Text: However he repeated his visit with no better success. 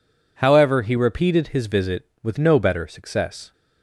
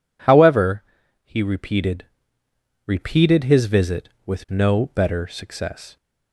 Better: first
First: none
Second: pauses between "However" and "he"; at 0.8 s; 0.42 s long // says "repeated" twice; at 2.8 s

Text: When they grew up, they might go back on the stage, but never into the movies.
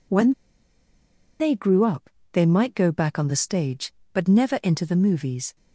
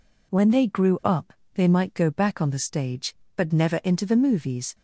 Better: second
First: pauses between "When" and "they"; at 0.3 s; 1.0 s long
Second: none

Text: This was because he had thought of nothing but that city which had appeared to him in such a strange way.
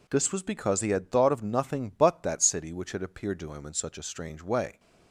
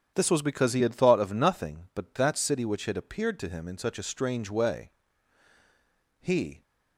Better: first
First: none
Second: starts louder than the rest; strong; until 1.1 s; 8.5 dB // goes on to say "He"; slight; from 6.2 s on; 0.42 s long

